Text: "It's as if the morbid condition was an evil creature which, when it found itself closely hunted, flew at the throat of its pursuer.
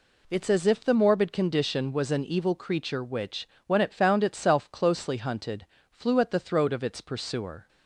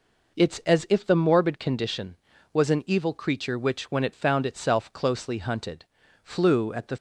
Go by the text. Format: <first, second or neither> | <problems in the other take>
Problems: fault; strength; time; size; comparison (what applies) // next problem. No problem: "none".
first | stops before "throat of its pursuer"; at 6.9 s